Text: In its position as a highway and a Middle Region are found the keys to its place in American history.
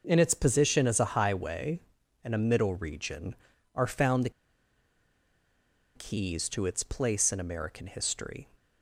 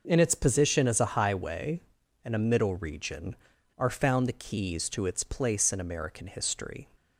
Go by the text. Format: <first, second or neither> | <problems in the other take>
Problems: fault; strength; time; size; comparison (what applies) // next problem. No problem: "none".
second | pauses between "the" and "keys"; strong; at 4.2 s; 1.6 s long